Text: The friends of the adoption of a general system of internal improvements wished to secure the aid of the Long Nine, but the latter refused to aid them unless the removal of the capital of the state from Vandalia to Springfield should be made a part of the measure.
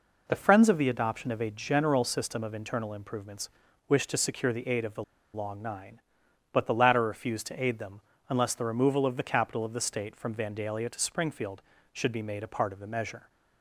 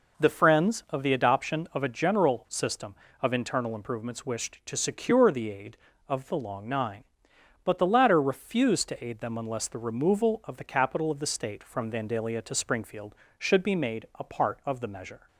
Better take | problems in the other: second | pauses between "improvements" and "wished"; at 3.4 s; 0.40 s long // pauses between "the" and "Long"; slight; at 5.0 s; 0.30 s long // pauses between "them" and "unless"; slight; at 8.0 s; 0.26 s long

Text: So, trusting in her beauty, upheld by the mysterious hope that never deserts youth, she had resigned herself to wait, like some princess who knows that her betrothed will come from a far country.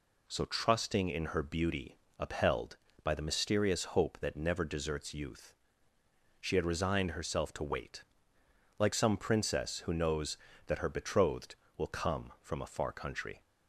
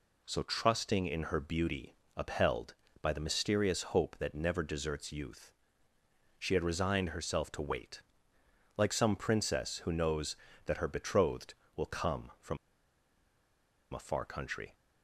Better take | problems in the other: first | pauses between "from" and "a"; strong; at 12.5 s; 1.3 s long

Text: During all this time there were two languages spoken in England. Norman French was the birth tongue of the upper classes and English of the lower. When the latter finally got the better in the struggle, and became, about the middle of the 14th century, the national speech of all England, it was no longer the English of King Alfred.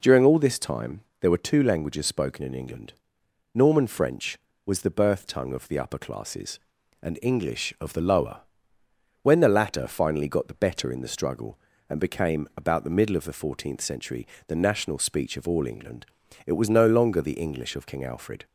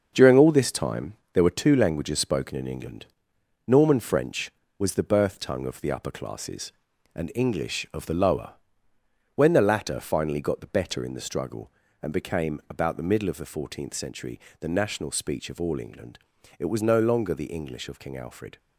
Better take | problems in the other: first | gets quieter; throughout; 6.5 dB // pauses between "time" and "there"; slight; at 1.1 s; 0.18 s long; slight in the first

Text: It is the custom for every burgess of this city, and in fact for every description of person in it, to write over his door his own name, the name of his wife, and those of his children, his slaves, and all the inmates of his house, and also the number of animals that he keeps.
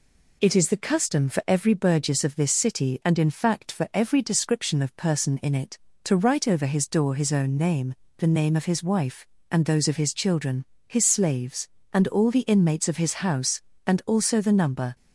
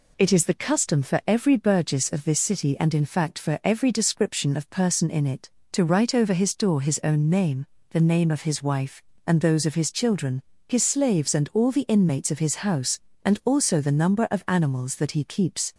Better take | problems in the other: second | stops before "of animals that he keeps"; at 14.9 s

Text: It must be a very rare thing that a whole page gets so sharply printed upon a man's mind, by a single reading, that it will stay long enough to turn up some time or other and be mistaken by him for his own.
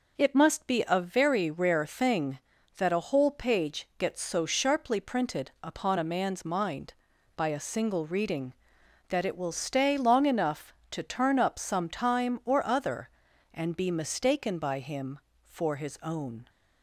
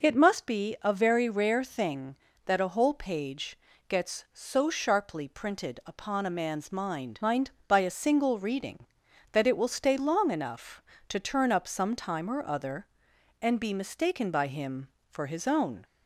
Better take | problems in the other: first | pauses between "page" and "gets"; slight; at 3.5 s; 0.32 s long // says "mind" twice; at 7.2 s

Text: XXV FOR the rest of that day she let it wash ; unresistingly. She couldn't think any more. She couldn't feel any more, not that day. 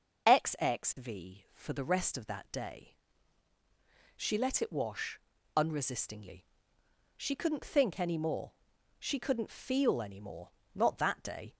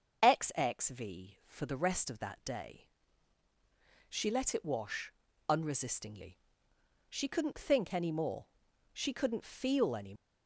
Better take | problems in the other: first | starts louder than the rest; until 1.2 s; 6.5 dB // pauses between "day" and "she"; at 2.8 s; 1.2 s long; also in the first // stops before "more not that day"; at 10.1 s

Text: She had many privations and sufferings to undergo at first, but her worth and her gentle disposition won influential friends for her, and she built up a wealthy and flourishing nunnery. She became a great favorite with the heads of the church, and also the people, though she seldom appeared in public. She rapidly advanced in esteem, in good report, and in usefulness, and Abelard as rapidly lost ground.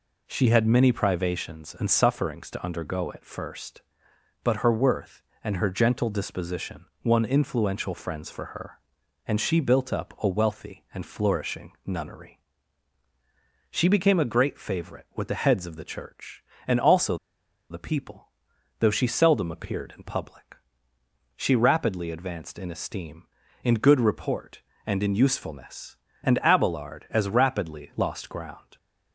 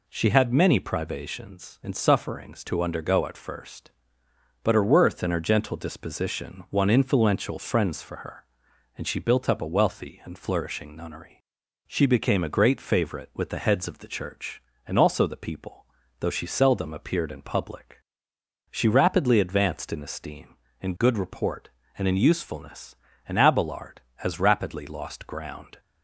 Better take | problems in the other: second | pauses between "disposition" and "won"; slight; at 6.8 s; 0.18 s long // pauses between "also" and "the"; noticeable; at 17.1 s; 0.55 s long

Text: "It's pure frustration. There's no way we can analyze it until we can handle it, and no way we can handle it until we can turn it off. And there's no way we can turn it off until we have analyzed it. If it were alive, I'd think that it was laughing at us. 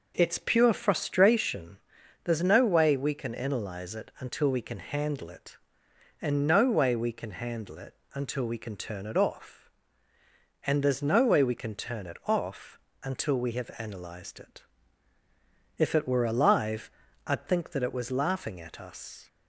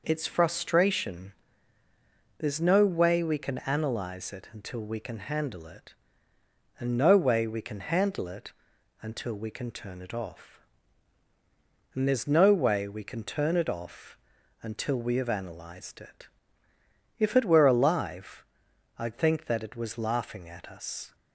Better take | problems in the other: first | skips "pure"; at 0.2 s // pauses between "it" and "until"; noticeable; at 8.5 s; 0.48 s long; slight in the first // pauses between "off" and "until"; at 14.1 s; 0.42 s long; slight in the first

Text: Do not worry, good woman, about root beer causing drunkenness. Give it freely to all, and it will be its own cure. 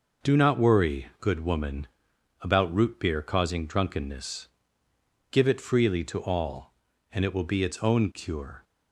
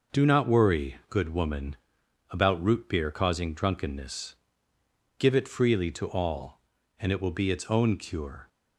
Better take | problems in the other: neither | none

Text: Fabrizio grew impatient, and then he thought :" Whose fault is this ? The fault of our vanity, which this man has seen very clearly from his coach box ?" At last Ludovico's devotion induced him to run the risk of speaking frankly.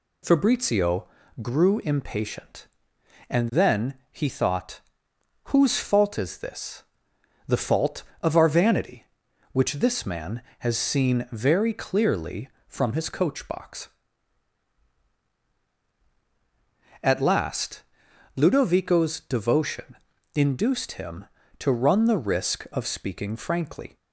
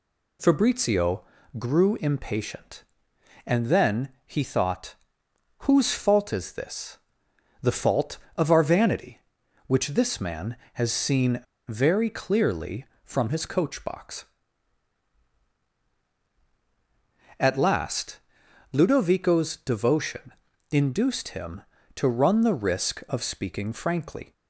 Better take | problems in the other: first | pauses between "Fabrizio" and "grew"; slight; at 1.2 s; 0.36 s long; slight in the first // pauses between "then" and "he"; slight; at 4.0 s; 0.18 s long; slight in the first // pauses between "seen" and "very"; slight; at 11.4 s; 0.24 s long // pauses between "last" and "Ludovico's"; noticeable; at 18.1 s; 0.54 s long; noticeable in the first // pauses between "devotion" and "induced"; at 20.3 s; 0.38 s long; also in the first

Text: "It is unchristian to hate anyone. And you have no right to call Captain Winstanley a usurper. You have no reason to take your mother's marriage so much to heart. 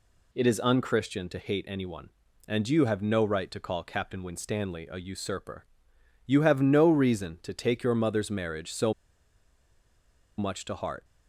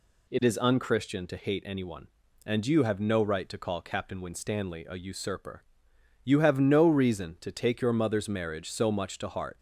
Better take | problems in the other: second | pauses between "so" and "much"; strong; at 8.9 s; 1.4 s long

